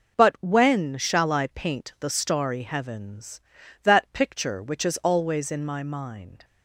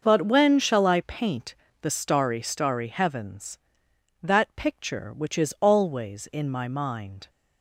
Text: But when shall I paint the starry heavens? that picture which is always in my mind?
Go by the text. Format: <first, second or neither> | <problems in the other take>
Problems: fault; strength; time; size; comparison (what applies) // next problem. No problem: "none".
first | starts louder than the rest; noticeable; until 1.0 s; 6 dB // pauses between "paint" and "the"; slight; at 1.5 s; 0.24 s long // says "starry" twice; at 2.4 s